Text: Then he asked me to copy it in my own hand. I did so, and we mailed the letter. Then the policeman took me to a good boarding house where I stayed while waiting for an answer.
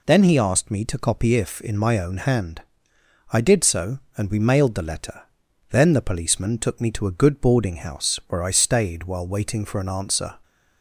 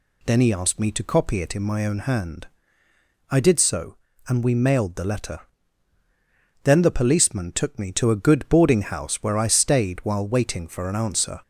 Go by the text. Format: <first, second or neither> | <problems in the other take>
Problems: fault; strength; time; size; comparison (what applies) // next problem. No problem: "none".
second | says "if" for "it"; at 1.3 s